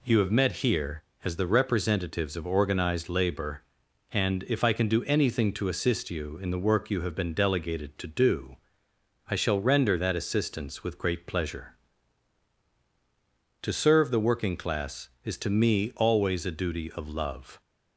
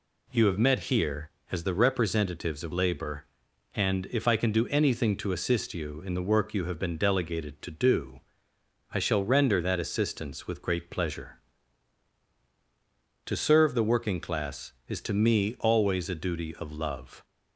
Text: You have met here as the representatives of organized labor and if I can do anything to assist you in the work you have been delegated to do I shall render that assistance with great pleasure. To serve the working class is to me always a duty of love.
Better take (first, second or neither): first